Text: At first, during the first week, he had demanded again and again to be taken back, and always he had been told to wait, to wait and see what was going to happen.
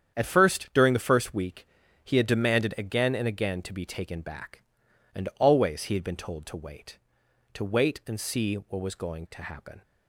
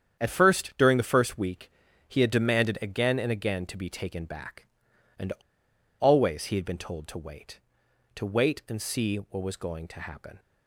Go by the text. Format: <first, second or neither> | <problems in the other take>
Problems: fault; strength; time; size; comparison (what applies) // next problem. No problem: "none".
first | starts louder than the rest; strong; until 1.2 s; 8.5 dB; strong in the first // pauses between "and" and "always"; noticeable; at 5.3 s; 0.69 s long